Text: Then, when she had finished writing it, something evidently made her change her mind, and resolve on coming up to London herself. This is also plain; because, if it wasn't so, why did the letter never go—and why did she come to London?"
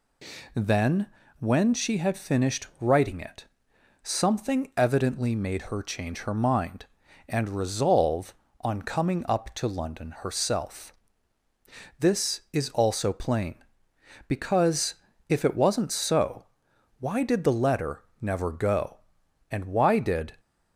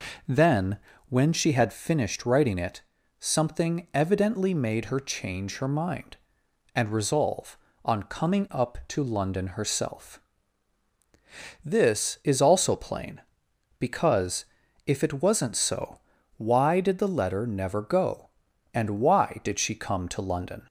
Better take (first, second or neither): second